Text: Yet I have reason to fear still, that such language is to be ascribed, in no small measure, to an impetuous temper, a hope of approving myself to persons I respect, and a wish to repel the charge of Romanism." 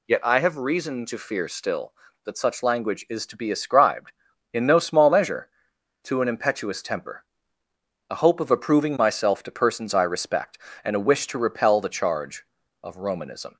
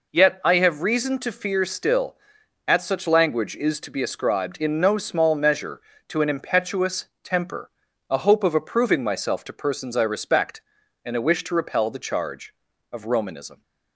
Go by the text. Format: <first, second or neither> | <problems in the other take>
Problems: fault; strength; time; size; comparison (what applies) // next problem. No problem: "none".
first | says "at" for "that"; at 2.6 s // pauses between "impetuous" and "temper"; slight; at 7.0 s; 0.16 s long